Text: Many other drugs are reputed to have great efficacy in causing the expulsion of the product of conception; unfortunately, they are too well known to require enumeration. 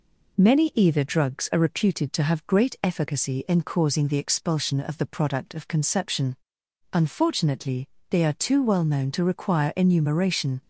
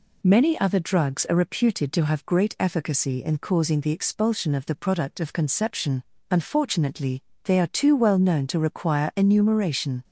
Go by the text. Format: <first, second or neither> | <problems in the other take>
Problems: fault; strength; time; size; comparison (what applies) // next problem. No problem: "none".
second | says "either" for "other"; at 0.7 s